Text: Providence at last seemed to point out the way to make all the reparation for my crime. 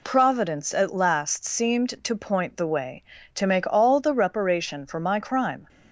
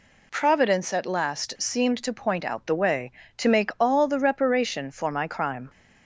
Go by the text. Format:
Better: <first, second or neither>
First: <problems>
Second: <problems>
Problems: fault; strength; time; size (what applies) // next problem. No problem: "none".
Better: second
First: skips "out"; at 2.5 s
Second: none